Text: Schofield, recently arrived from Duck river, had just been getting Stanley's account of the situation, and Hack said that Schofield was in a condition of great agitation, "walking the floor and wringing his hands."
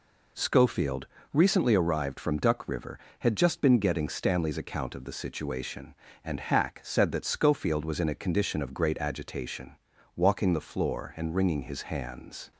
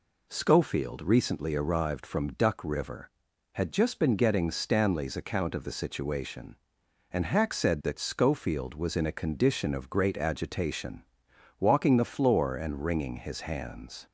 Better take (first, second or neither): neither